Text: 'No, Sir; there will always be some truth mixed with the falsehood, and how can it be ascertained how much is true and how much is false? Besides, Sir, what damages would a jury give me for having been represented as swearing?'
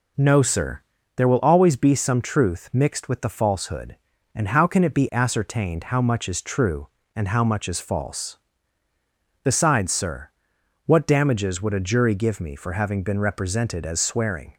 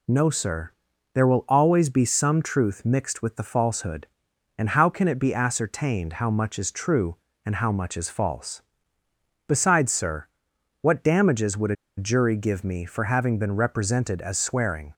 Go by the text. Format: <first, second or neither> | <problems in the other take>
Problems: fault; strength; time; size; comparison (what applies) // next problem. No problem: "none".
first | pauses between "a" and "jury"; slight; at 11.7 s; 0.22 s long